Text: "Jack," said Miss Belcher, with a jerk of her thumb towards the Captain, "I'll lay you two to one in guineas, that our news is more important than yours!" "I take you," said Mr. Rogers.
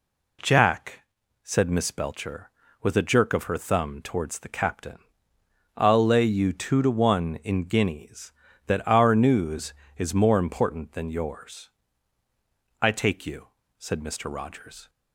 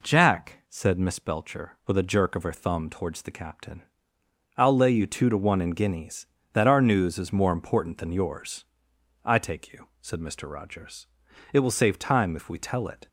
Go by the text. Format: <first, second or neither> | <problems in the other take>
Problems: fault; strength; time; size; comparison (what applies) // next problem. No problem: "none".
first | goes on to say "It will save time if we tell it"; from 11.5 s on; 1.5 s long